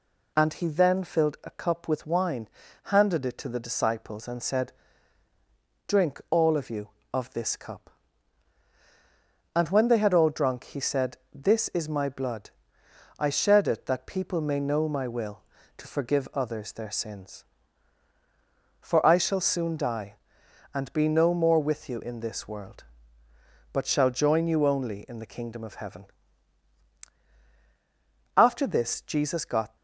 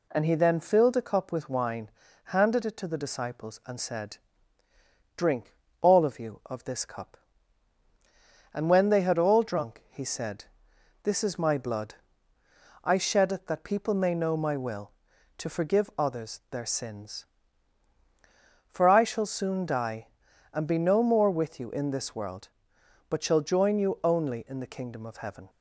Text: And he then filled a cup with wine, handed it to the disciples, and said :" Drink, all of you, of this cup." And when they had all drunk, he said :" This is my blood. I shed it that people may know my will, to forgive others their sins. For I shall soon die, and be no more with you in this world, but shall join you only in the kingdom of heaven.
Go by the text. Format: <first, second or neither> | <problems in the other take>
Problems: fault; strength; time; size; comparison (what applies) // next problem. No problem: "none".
second | goes on to say "After this Jesus got"; from 28.3 s on; 1.3 s long